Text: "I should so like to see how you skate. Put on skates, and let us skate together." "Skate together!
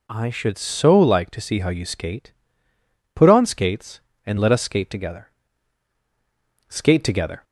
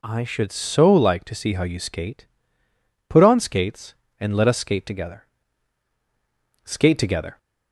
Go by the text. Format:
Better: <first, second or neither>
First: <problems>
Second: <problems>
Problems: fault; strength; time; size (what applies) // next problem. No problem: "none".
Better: neither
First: none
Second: none